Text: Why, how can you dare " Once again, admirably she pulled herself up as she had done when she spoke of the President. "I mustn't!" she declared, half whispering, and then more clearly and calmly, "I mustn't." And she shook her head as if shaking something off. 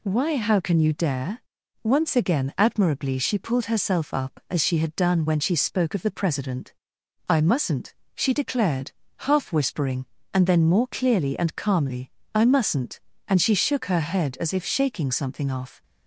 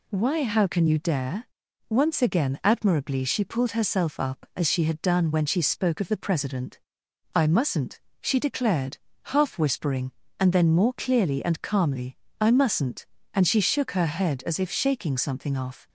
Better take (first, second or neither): neither